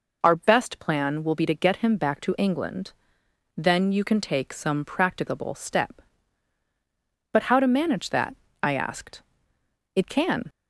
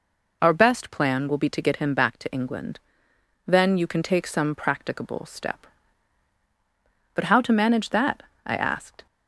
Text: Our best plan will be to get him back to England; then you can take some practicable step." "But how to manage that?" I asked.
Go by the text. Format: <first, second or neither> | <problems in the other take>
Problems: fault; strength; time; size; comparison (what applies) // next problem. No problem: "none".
second | goes on to say "It can"; from 9.9 s on; 0.54 s long